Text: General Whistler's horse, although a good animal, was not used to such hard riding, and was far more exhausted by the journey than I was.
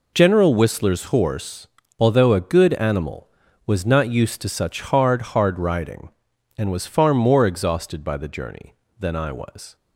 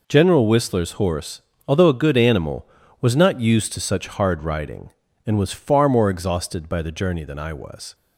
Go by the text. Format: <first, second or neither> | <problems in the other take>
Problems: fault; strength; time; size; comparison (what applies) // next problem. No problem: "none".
second | says "hard" twice; at 5.3 s